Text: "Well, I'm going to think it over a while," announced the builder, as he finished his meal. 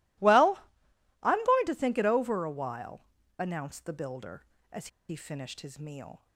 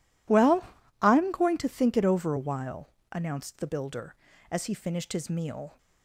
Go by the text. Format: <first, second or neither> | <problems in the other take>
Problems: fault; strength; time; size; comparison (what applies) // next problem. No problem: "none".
second | pauses between "as" and "he"; slight; at 4.8 s; 0.21 s long